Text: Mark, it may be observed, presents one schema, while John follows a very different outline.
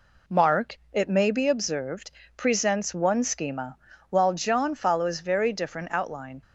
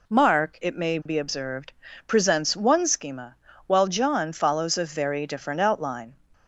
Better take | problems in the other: second | skips "a"; at 5.1 s

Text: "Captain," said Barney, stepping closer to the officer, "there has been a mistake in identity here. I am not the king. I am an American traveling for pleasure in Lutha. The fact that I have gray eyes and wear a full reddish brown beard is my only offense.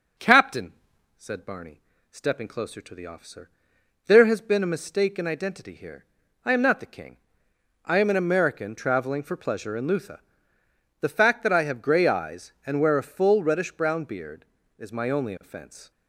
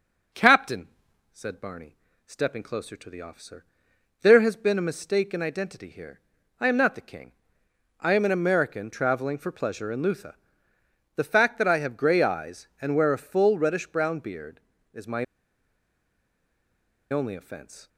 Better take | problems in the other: first | pauses between "my" and "only"; strong; at 15.2 s; 1.8 s long

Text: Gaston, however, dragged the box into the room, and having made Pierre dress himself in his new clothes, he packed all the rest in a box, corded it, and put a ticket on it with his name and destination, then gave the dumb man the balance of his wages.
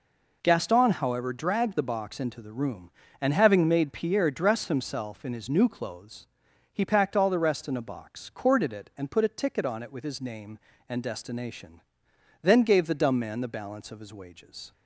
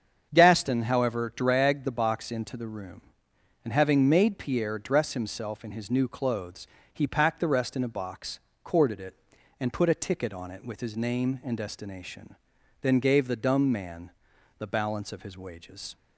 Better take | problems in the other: first | starts louder than the rest; strong; until 1.3 s; 7.5 dB // skips "all"; at 7.3 s // pauses between "man" and "the"; noticeable; at 14.1 s; 0.48 s long

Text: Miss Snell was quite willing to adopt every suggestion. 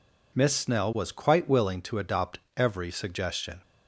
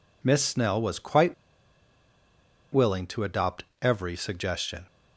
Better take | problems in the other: first | pauses between "quite" and "willing"; strong; at 1.3 s; 1.3 s long // pauses between "adopt" and "every"; slight; at 3.6 s; 0.18 s long; slight in the first

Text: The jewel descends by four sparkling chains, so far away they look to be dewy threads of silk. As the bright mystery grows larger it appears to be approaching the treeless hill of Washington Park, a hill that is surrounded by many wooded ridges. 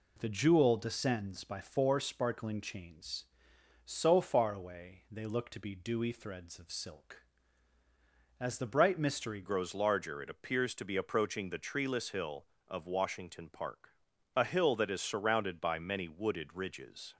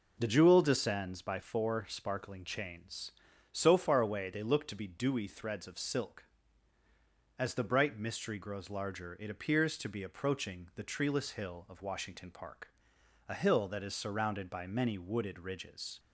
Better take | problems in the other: second | changes voice at "grows"; from 9.4 s on; 7.7 s long

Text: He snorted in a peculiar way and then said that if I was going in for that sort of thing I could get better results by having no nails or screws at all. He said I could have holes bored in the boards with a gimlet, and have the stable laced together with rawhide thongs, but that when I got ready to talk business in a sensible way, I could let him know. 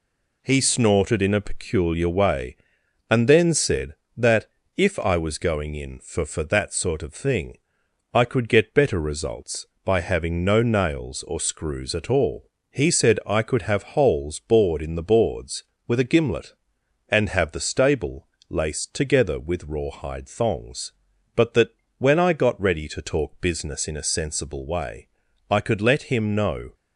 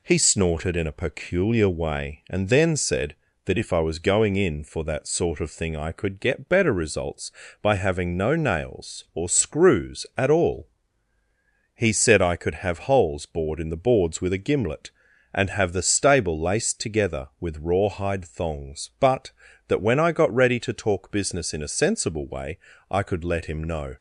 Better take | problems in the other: second | pauses between "that" and "if"; slight; at 4.4 s; 0.30 s long // says "for" twice; at 6.2 s // pauses between "thing" and "I"; noticeable; at 7.5 s; 0.56 s long // pauses between "stable" and "laced"; slight; at 18.2 s; 0.20 s long // pauses between "that" and "when"; slight; at 21.6 s; 0.28 s long

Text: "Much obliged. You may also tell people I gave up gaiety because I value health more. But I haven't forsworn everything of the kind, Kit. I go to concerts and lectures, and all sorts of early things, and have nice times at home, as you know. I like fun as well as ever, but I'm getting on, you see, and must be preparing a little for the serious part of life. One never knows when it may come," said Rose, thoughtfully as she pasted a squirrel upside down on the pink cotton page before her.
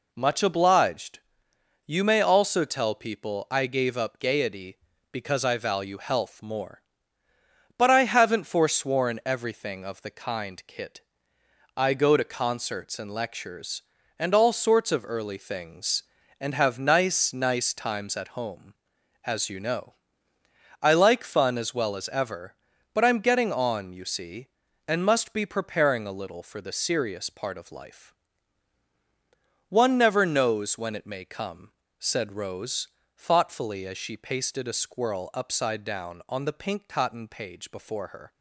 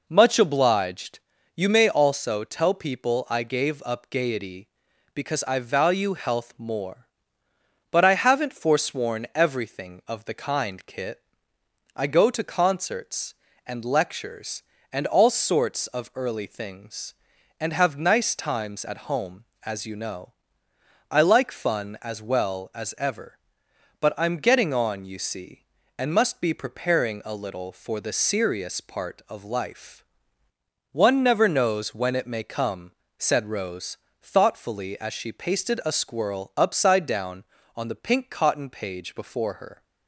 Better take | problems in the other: second | says "nice" twice; at 17.3 s

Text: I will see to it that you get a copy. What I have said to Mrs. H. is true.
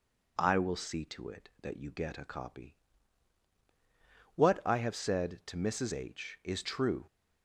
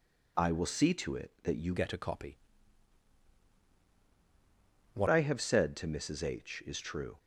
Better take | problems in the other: first | changes voice from "get" to "What"; from 1.7 to 5.0 s; 3.3 s long

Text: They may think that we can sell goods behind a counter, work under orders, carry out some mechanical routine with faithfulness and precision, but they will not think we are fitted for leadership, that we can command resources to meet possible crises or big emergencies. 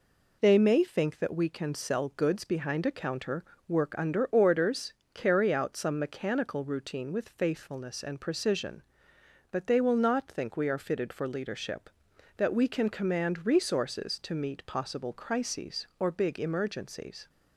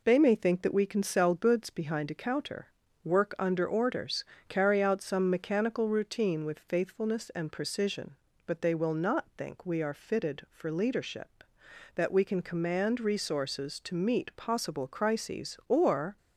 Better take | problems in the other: first | stops before "big emergencies"; at 16.1 s

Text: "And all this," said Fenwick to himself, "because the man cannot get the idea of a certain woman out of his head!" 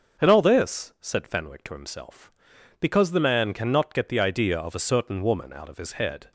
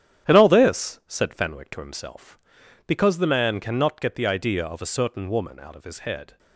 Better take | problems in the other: first | gets quieter; strong; throughout; 8 dB // starts louder than the rest; strong; until 1.3 s; 10 dB; also in the first

